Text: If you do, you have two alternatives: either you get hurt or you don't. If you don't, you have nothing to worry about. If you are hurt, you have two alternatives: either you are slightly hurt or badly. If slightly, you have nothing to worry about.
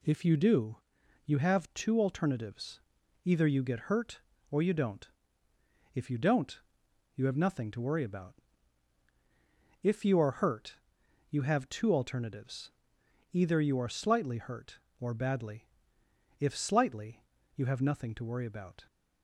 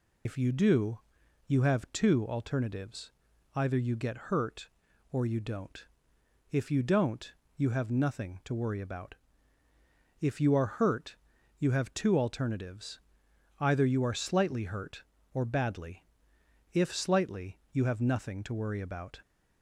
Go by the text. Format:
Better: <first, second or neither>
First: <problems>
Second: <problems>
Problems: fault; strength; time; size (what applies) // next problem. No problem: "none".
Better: first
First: none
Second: loses the start of "If"; at 0.2 s; 60 ms